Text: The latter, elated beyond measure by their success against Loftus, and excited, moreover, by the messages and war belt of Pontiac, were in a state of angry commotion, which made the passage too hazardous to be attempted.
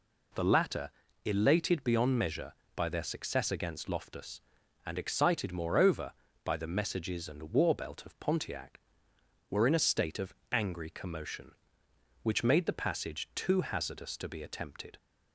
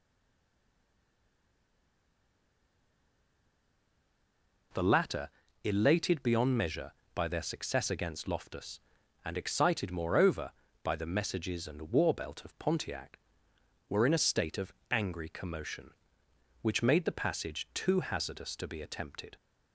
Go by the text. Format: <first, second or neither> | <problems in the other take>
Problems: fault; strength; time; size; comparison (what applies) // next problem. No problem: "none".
first | stays silent before the first word; strong; until 4.7 s; 4.7 s long // pauses between "of" and "angry"; slight; at 14.7 s; 0.18 s long; slight in the first